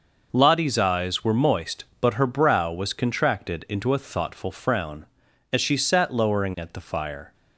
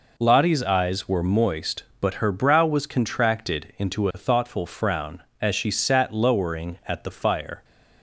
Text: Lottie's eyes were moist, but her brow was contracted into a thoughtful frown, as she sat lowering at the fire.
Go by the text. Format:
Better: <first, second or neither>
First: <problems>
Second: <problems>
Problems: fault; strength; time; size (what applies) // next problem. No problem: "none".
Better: neither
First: none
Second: none